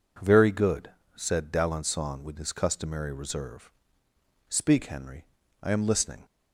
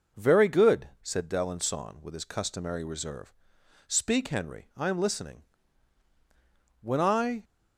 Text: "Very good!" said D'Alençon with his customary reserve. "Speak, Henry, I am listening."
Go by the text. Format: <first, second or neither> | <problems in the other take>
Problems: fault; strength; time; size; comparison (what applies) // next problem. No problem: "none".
first | goes on to say "When I"; noticeable; from 6.8 s on; 0.62 s long